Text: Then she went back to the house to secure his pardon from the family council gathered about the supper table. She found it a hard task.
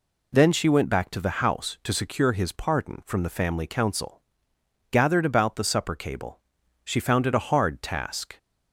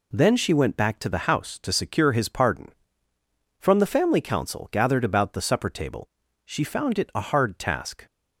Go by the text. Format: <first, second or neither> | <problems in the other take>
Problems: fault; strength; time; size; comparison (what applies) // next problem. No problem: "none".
second | pauses between "council" and "gathered"; noticeable; at 4.1 s; 0.70 s long // says "cable" for "table"; at 5.9 s